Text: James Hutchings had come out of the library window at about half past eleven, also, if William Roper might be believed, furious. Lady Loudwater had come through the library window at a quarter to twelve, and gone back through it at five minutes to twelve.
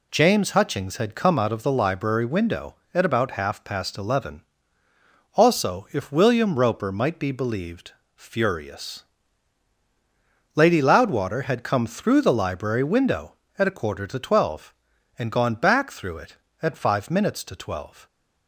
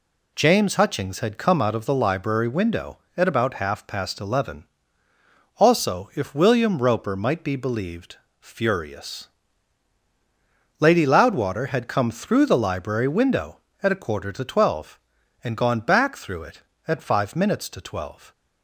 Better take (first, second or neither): neither